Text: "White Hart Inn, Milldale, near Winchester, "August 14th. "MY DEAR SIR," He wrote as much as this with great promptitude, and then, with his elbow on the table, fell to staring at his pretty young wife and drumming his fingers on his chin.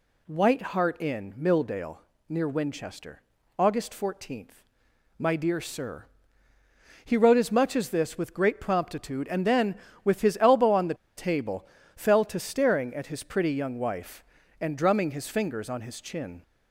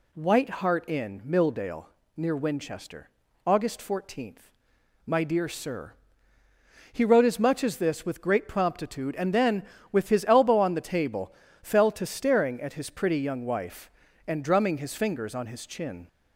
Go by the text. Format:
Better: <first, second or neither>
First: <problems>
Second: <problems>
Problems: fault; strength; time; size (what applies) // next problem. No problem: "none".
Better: second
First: pauses between "the" and "table"; slight; at 10.9 s; 0.22 s long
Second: none